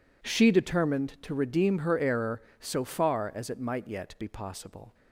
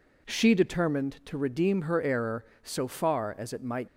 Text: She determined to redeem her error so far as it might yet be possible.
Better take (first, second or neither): first